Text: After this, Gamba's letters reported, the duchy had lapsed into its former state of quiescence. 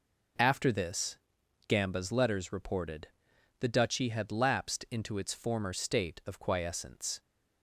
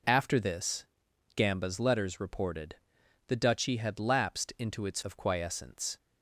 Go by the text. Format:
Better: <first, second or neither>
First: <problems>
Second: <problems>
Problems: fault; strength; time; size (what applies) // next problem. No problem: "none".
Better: first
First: none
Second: skips "former state"; at 5.0 s